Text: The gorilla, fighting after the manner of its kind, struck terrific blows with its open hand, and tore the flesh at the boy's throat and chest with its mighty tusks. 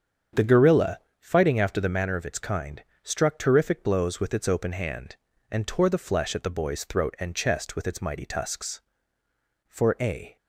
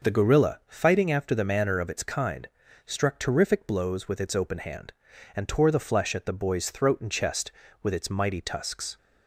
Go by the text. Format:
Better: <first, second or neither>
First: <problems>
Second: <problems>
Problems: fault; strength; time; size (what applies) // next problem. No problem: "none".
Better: second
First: starts louder than the rest; strong; until 1.5 s; 7.5 dB // goes on to say "For a"; noticeable; from 9.6 s on; 0.68 s long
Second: none